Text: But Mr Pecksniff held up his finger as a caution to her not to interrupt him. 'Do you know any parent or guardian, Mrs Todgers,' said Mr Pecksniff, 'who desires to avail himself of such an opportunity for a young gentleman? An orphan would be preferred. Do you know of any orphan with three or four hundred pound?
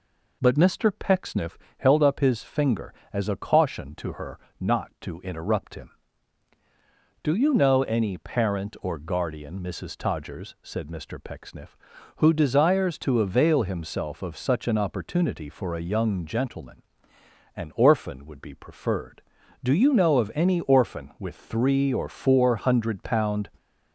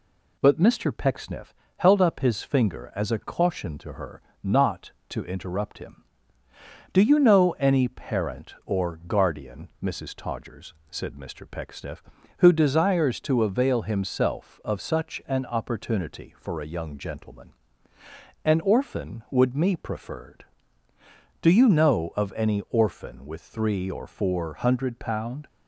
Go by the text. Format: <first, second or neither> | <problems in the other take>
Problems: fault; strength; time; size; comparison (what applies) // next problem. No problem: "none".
first | pauses between "Pecksniff" and "held"; slight; at 1.5 s; 0.24 s long; slight in the first // pauses between "her" and "not"; slight; at 4.2 s; 0.22 s long; slight in the first // says "me" for "be"; at 19.5 s